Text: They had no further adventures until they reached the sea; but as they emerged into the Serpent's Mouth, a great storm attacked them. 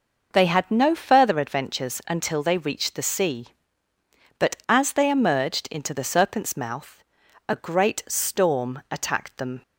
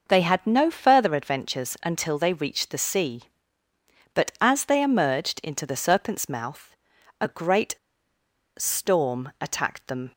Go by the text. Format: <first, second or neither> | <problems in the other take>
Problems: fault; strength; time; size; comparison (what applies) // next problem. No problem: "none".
first | pauses between "great" and "storm"; noticeable; at 7.7 s; 0.83 s long